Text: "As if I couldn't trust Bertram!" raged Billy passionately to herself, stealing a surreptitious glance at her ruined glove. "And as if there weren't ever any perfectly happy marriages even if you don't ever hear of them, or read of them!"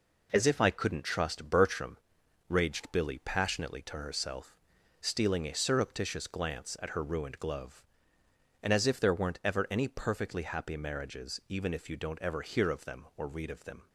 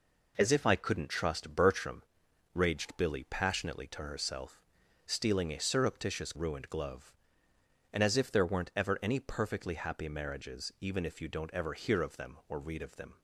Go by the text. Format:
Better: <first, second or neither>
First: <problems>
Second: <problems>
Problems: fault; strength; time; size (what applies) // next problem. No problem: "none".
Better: first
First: none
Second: skips "glance at her"; at 6.3 s